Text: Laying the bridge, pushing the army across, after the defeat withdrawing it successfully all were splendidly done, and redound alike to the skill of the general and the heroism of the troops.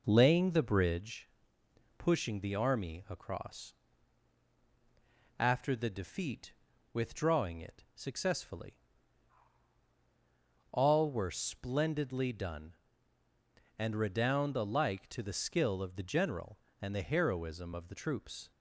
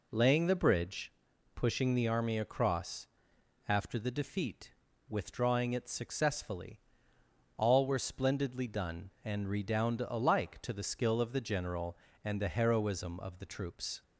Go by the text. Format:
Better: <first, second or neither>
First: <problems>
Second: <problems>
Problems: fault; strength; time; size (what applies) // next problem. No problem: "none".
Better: second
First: starts louder than the rest; noticeable; until 1.0 s; 5 dB // pauses between "defeat" and "withdrawing"; at 6.5 s; 0.40 s long // pauses between "successfully" and "all"; strong; at 8.7 s; 1.9 s long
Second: pauses between "defeat" and "withdrawing"; at 4.7 s; 0.38 s long // pauses between "successfully" and "all"; noticeable; at 6.7 s; 0.78 s long